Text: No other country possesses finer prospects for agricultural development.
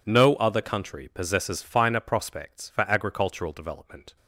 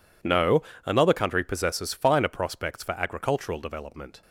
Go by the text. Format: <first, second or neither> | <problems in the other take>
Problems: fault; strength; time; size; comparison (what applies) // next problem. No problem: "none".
first | says "another" for "other"; at 0.8 s